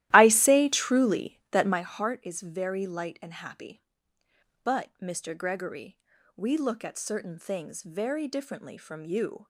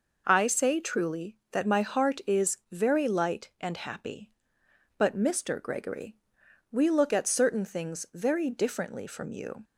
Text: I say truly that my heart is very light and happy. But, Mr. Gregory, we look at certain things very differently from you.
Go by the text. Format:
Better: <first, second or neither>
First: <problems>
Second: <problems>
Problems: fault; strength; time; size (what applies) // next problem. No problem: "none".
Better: second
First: starts louder than the rest; strong; until 1.9 s; 14.5 dB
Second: none